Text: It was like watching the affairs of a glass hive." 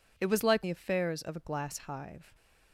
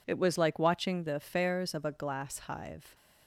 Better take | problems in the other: second | skips "watching"; at 0.6 s

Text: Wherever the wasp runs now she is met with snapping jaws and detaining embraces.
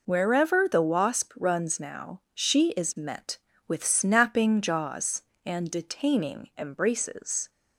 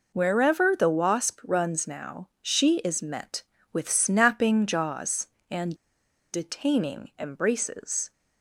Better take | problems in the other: first | pauses between "and" and "detaining"; noticeable; at 5.7 s; 0.59 s long

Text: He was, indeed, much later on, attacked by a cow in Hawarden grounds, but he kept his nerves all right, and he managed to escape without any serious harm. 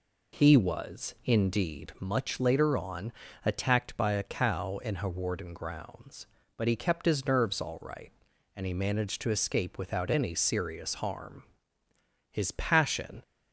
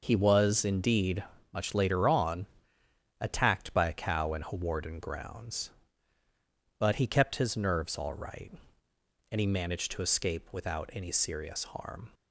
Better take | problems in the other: second | goes on to say "His passion"; noticeable; from 12.3 s on; 0.90 s long

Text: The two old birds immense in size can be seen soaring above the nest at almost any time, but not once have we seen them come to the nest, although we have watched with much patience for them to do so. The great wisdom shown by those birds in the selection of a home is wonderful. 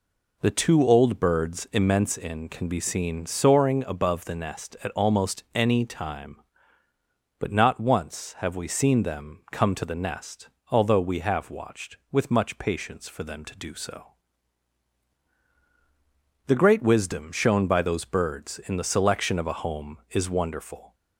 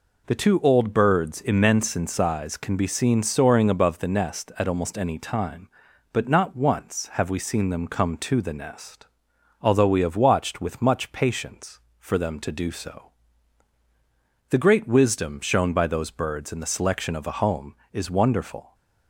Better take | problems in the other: second | skips "size"; at 2.4 s

